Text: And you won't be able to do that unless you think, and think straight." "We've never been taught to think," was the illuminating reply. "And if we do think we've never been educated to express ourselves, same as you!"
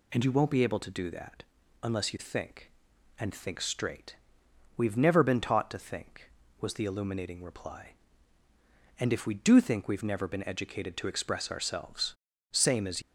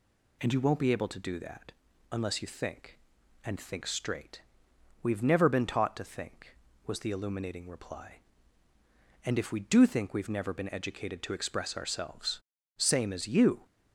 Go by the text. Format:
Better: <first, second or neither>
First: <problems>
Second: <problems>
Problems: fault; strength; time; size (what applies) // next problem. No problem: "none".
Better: second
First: pauses between "that" and "unless"; at 1.4 s; 0.38 s long // stops before "you"; at 13.0 s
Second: pauses between "that" and "unless"; at 1.7 s; 0.38 s long